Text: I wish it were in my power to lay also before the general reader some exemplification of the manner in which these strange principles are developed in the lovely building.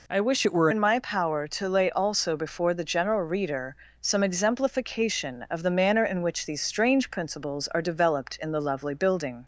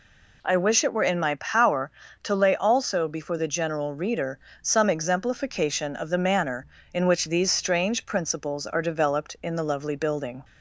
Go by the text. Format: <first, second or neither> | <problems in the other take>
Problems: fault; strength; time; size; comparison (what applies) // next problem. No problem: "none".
second | changes voice from "it" to "were"; from 0.4 to 0.6 s; 0.2 s long // pauses between "reader" and "some"; slight; at 3.7 s; 0.24 s long; slight in the second